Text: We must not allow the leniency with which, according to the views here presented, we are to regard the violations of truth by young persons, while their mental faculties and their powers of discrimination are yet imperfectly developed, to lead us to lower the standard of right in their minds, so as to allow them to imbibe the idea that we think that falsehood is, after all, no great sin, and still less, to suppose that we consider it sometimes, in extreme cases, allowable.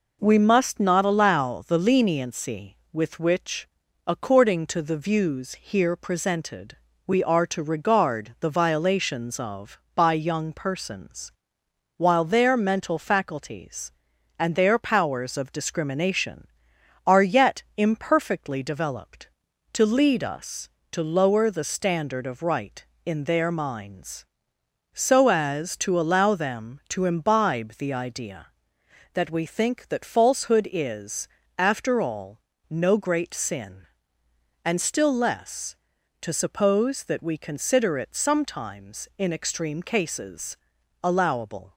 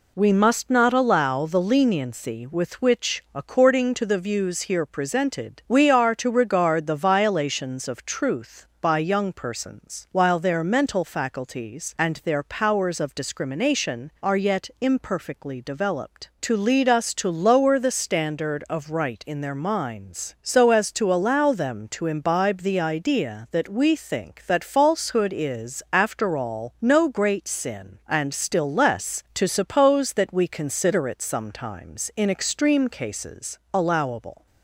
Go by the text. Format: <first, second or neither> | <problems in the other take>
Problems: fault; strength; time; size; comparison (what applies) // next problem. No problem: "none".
second | skips "truth"; at 9.8 s // pauses between "yet" and "imperfectly"; slight; at 17.6 s; 0.16 s long